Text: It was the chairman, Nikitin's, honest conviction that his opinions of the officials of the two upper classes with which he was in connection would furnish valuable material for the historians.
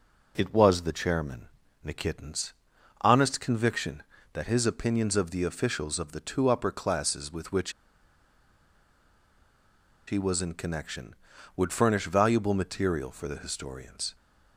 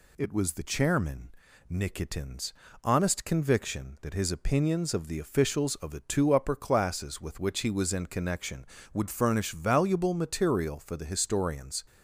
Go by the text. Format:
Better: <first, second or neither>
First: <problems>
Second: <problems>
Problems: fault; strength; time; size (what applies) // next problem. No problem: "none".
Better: second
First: pauses between "which" and "he"; strong; at 7.7 s; 2.3 s long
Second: none